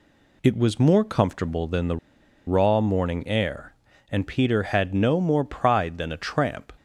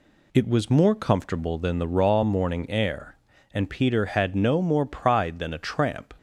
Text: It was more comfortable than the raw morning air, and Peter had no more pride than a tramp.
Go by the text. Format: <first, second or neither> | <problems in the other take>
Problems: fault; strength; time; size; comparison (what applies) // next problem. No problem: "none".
second | pauses between "the" and "raw"; noticeable; at 1.9 s; 0.49 s long